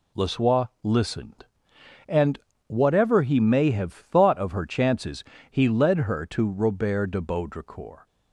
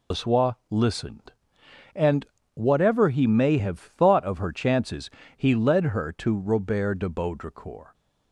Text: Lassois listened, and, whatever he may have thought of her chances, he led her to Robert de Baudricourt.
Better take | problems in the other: first | loses the start of "Lassois"; at 0.1 s; 85 ms // pauses between "Lassois" and "listened"; slight; at 0.5 s; 0.16 s long; slight in the first

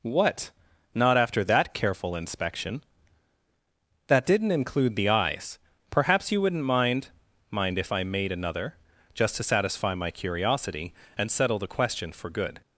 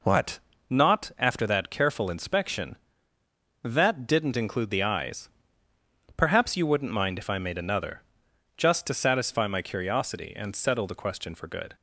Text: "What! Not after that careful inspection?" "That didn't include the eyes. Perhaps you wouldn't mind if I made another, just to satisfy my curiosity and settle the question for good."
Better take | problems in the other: second | says "mind" twice; at 7.5 s

